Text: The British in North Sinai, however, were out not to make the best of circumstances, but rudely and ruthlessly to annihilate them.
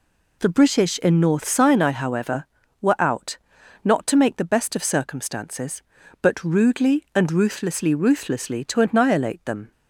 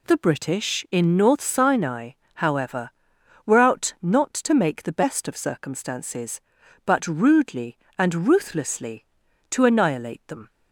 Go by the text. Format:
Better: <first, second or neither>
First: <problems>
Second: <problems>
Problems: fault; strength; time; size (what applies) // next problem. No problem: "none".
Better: second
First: pauses between "out" and "not"; at 3.3 s; 0.44 s long // says "ruthlessly" twice; at 7.9 s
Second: none